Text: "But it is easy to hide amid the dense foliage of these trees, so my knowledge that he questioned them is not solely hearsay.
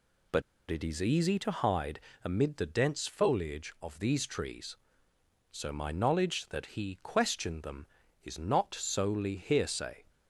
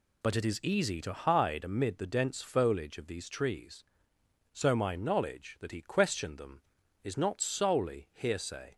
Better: second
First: pauses between "But" and "it"; slight; at 0.4 s; 0.28 s long // pauses between "hide" and "amid"; slight; at 1.9 s; 0.24 s long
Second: none

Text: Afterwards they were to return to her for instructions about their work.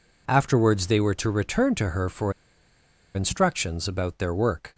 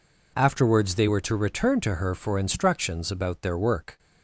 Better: second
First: pauses between "for" and "instructions"; noticeable; at 2.3 s; 0.82 s long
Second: none

